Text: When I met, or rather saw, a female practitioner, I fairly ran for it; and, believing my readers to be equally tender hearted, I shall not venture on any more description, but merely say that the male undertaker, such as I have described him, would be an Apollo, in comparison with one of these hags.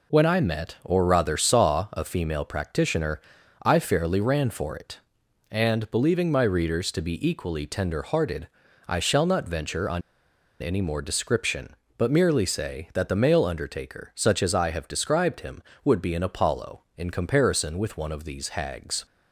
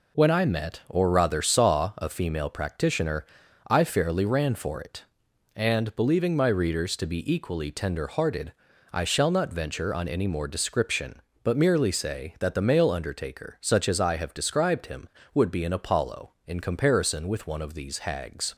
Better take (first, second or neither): second